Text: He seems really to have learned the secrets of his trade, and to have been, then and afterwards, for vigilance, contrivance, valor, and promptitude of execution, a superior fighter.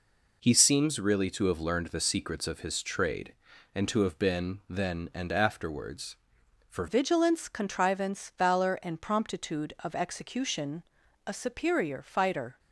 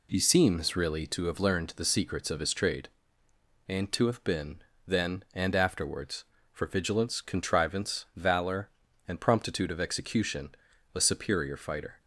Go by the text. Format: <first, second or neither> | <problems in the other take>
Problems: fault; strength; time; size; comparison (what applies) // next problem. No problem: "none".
second | changes voice at "vigilance"; from 6.8 s on; 5.7 s long